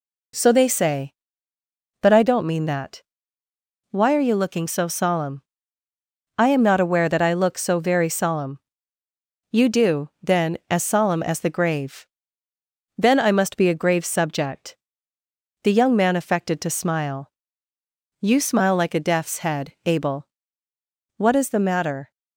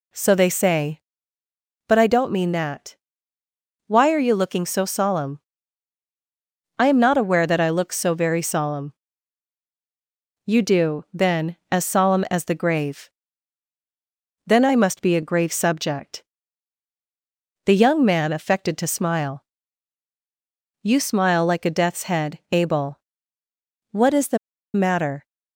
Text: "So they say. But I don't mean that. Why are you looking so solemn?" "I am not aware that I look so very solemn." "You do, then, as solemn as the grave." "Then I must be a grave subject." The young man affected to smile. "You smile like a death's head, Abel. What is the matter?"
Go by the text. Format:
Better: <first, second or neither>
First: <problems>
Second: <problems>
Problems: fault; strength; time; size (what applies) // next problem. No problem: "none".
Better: first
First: none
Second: pauses between "the" and "matter"; at 24.3 s; 0.37 s long